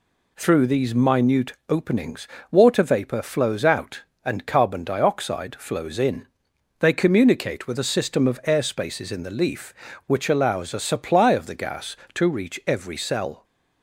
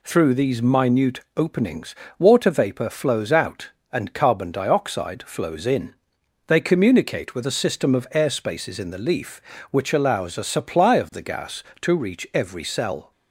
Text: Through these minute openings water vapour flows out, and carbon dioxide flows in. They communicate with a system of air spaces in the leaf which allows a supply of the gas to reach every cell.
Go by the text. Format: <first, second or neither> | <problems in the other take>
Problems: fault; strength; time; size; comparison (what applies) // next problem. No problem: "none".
neither | pauses between "minute" and "openings"; slight; the same in both // pauses between "openings" and "water"; slight; the same in both